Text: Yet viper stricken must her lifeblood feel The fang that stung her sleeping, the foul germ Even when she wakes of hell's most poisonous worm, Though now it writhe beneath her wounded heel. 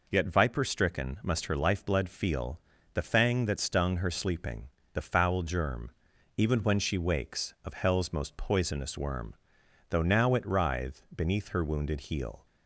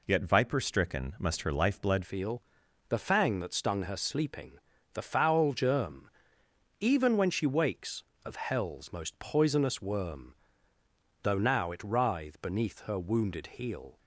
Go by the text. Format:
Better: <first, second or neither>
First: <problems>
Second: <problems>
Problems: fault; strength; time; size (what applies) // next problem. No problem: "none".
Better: first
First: pauses between "feel" and "The"; slight; at 2.5 s; 0.34 s long // pauses between "germ" and "Even"; noticeable; at 5.9 s; 0.46 s long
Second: changes voice at "feel"; from 2.0 s on; 11.9 s long // pauses between "feel" and "The"; noticeable; at 2.4 s; 0.48 s long // pauses between "germ" and "Even"; noticeable; at 6.1 s; 0.70 s long